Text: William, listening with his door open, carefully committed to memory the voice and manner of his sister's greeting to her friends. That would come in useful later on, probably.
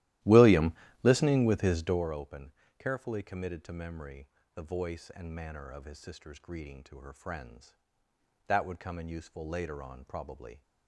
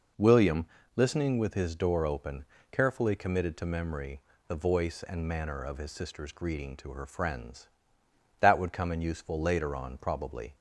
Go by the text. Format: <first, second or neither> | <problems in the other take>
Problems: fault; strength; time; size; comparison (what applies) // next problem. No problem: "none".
second | starts louder than the rest; strong; until 2.1 s; 15 dB // pauses between "memory" and "the"; slight; at 4.2 s; 0.26 s long; slight in the second